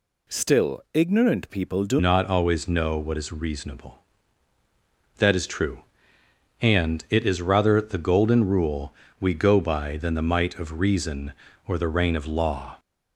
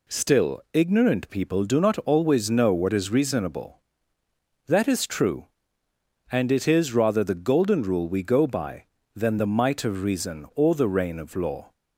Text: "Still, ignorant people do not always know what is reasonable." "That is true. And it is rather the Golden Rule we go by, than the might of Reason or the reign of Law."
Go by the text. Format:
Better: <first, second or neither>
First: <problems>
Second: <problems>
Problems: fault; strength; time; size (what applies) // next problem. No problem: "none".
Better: second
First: changes voice at "not"; from 1.9 s on; 10.8 s long // pauses between "Rule" and "we"; slight; at 8.9 s; 0.26 s long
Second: none